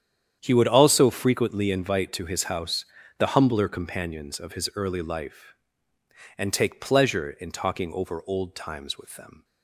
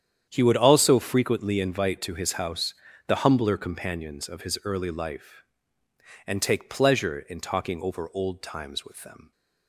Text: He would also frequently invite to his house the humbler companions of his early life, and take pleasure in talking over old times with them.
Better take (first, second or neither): neither